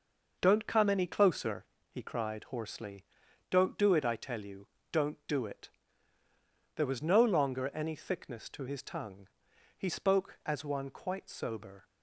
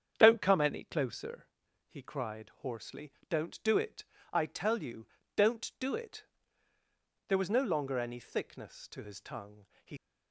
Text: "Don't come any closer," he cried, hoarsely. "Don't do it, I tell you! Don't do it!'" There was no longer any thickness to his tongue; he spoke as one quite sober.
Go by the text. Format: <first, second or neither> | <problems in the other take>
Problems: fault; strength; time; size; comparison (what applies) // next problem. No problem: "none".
first | starts louder than the rest; strong; until 1.1 s; 8 dB // stops before "spoke as one quite sober"; at 9.9 s